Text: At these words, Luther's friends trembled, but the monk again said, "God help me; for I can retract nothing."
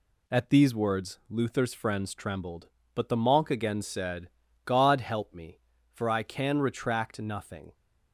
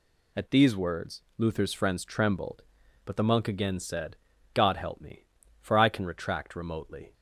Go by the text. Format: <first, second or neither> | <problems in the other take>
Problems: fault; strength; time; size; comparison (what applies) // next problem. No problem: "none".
first | says "remotely" for "nothing"; at 6.5 s